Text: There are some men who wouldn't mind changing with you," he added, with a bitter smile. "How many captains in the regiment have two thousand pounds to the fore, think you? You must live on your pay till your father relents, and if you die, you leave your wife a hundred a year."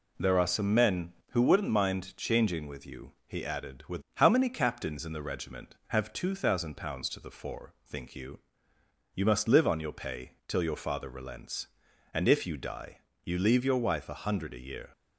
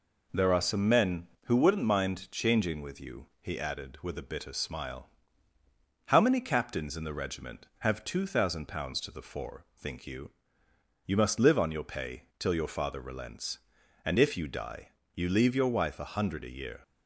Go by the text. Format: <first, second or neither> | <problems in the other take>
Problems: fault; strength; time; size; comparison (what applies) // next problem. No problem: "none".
second | skips "a bitter smile"; at 4.0 s